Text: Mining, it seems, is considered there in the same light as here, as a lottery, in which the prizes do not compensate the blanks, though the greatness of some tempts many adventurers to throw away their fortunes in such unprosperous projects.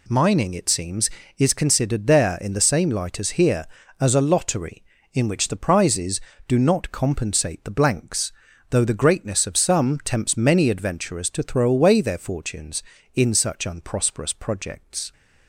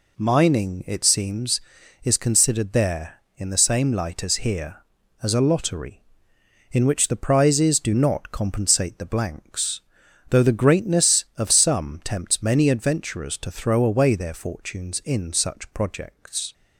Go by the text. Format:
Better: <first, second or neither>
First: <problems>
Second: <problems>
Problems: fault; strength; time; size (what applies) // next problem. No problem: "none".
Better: first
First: none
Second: skips "unprosperous"; at 15.7 s